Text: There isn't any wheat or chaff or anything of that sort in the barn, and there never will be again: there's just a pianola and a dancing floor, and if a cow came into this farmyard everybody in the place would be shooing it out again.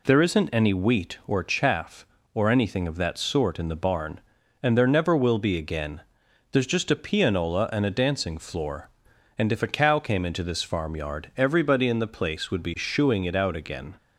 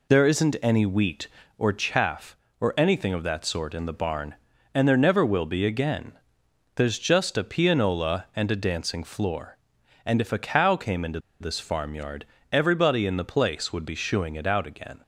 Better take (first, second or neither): first